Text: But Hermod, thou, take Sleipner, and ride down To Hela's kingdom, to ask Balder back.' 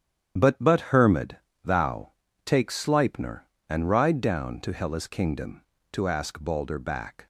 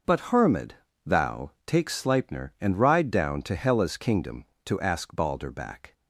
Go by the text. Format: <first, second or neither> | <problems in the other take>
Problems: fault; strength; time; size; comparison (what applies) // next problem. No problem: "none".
second | starts louder than the rest; strong; until 1.6 s; 9.5 dB // says "But" twice; at 0.6 s